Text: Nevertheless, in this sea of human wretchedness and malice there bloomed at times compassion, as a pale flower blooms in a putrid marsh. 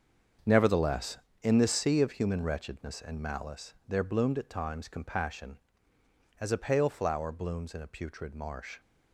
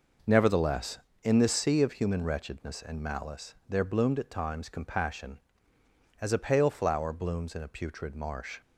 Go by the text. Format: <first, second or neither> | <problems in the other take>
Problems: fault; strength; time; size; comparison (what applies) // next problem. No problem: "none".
second | gets quieter; strong; throughout; 11 dB